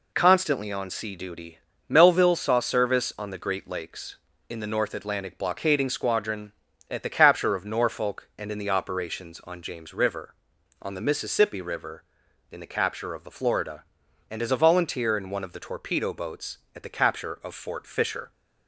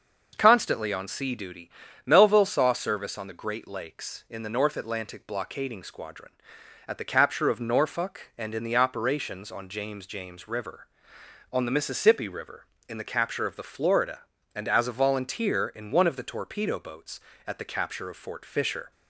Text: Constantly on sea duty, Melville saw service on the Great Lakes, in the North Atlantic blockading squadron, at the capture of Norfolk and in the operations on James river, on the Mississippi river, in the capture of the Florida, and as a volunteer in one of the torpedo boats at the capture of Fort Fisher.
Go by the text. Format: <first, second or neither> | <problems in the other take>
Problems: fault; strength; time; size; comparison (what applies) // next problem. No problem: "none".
first | says "James" twice; at 10.0 s